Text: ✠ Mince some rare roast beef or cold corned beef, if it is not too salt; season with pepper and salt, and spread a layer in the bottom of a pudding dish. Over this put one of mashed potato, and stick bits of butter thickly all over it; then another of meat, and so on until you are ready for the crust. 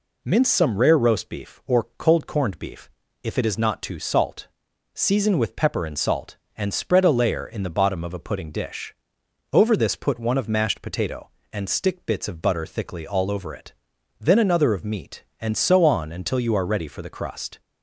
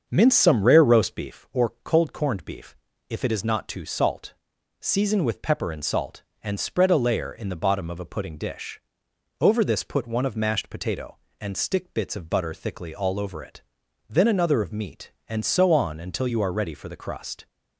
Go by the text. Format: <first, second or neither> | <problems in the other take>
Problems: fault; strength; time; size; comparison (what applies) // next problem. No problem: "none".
first | starts louder than the rest; until 1.4 s; 6.5 dB